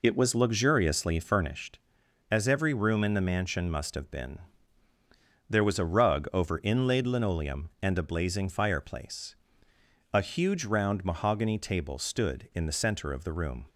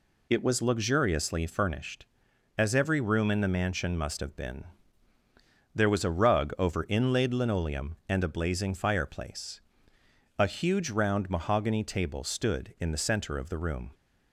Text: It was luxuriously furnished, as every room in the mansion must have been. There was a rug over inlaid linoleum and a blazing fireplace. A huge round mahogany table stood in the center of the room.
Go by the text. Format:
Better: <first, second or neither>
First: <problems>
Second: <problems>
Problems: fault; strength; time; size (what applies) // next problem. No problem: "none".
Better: second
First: starts louder than the rest; until 1.6 s; 3.5 dB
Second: none